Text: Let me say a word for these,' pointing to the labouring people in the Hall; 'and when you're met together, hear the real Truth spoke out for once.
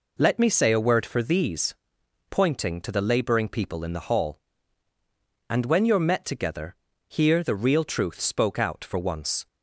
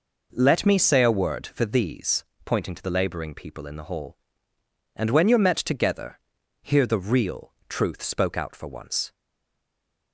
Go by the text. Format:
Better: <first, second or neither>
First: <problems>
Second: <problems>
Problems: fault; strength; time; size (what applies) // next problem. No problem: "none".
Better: first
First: none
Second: pauses between "real" and "Truth"; slight; at 7.5 s; 0.16 s long // stays silent after the last word; from 9.1 s on; 1.0 s long